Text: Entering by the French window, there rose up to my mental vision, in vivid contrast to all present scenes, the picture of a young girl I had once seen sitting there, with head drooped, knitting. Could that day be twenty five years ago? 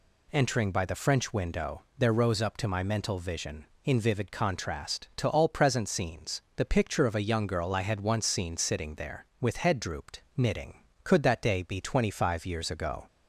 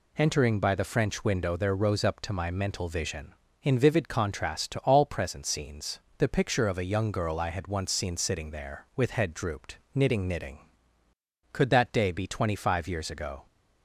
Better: first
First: none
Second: says "knitting" twice; at 10.2 s

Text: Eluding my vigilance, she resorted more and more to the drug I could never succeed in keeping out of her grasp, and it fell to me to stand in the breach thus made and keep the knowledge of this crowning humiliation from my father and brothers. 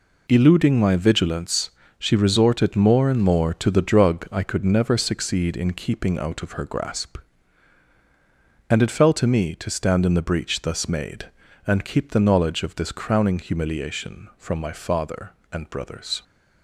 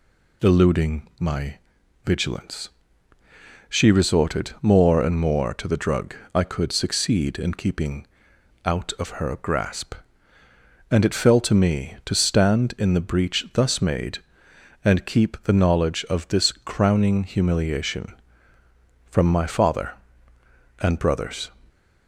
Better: first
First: none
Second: pauses between "my" and "vigilance"; noticeable; at 1.5 s; 0.50 s long // pauses between "drug" and "I"; slight; at 6.1 s; 0.20 s long // skips "never"; at 6.7 s // pauses between "keeping" and "out"; noticeable; at 8.0 s; 0.58 s long

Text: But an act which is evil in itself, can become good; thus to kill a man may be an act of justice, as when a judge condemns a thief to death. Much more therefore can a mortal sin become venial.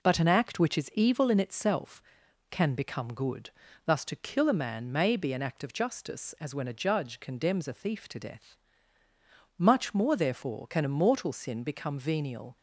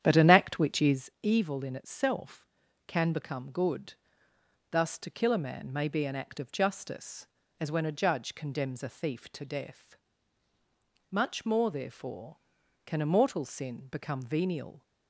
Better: first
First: none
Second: starts louder than the rest; strong; until 1.2 s; 9.5 dB

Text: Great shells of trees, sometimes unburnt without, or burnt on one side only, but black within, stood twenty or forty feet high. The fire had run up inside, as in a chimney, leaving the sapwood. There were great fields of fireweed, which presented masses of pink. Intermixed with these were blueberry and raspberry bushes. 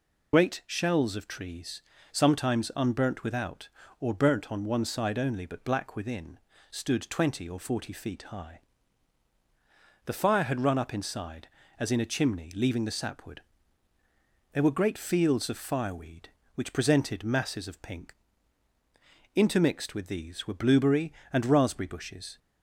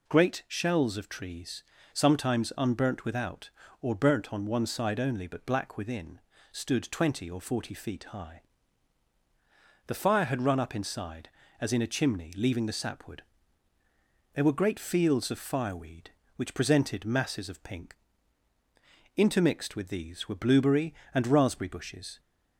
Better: second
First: loses the start of "Great"; at 0.3 s; 70 ms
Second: none

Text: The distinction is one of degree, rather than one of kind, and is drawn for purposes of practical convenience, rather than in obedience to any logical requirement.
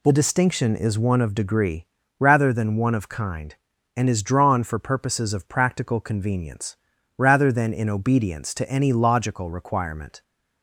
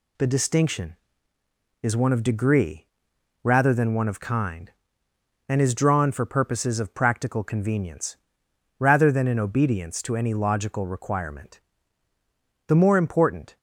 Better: first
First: none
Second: goes on to say "The more important"; noticeable; from 12.6 s on; 0.90 s long

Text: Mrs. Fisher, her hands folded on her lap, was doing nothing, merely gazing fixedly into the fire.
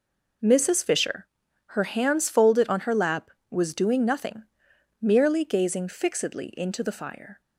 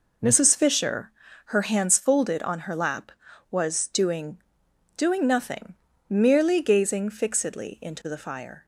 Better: first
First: none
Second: says "doing" twice; at 4.9 s

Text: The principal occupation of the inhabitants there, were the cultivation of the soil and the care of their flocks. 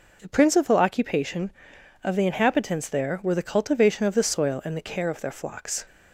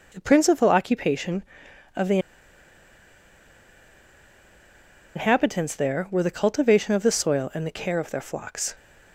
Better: first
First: none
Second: pauses between "the" and "inhabitants"; strong; at 2.1 s; 2.9 s long

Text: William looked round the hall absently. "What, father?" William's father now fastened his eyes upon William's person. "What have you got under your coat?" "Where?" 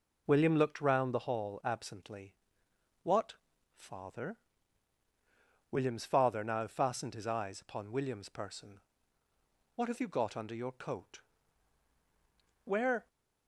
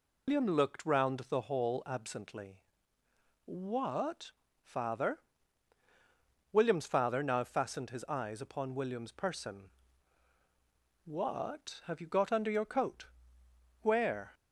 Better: first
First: none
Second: loses the start of "William"; at 0.2 s; 130 ms

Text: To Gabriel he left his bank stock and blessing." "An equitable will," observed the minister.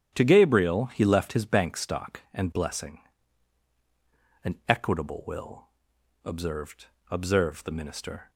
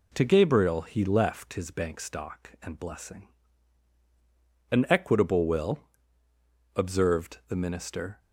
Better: second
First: starts louder than the rest; strong; until 1.1 s; 9.5 dB // says "observed" twice; at 7.0 s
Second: none

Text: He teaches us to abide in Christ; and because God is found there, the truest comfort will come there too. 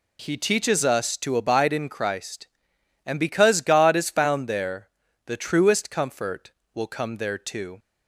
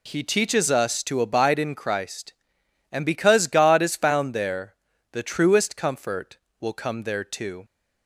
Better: neither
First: none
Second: none

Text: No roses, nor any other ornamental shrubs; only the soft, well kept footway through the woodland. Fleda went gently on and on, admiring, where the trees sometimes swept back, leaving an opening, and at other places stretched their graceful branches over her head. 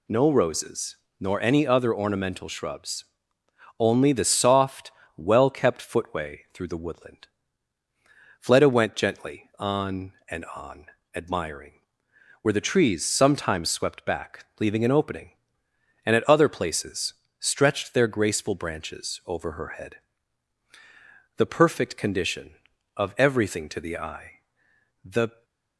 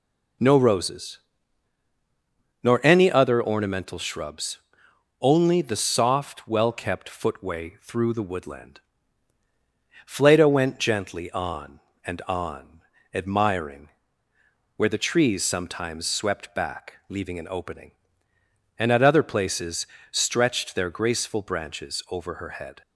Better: second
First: pauses between "places" and "stretched"; slight; at 17.1 s; 0.24 s long // goes on to say "The perfect condition of everything to the eye the"; strong; from 21.3 s on; 4.0 s long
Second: pauses between "places" and "stretched"; slight; at 19.8 s; 0.26 s long

